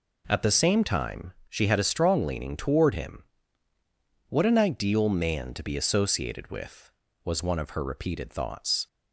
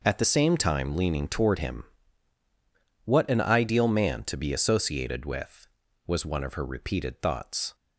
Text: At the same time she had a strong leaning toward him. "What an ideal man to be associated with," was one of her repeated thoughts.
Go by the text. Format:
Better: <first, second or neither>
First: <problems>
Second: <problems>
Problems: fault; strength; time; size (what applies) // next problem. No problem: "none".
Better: first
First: none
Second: skips "she had a strong"; at 0.9 s